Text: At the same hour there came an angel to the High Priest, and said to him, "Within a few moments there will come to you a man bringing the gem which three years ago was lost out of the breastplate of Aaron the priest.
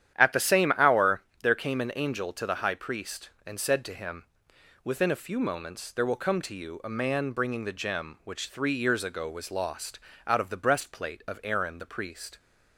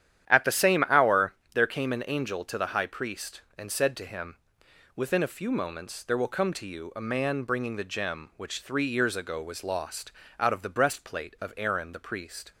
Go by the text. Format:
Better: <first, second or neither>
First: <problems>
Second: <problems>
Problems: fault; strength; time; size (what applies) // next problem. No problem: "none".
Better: neither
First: starts louder than the rest; strong; until 1.2 s; 10.5 dB // pauses between "hour" and "there"; slight; at 1.2 s; 0.20 s long // pauses between "lost" and "out"; slight; at 10.0 s; 0.26 s long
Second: starts louder than the rest; strong; until 1.3 s; 10.5 dB // pauses between "hour" and "there"; slight; at 1.3 s; 0.20 s long // pauses between "lost" and "out"; slight; at 10.1 s; 0.26 s long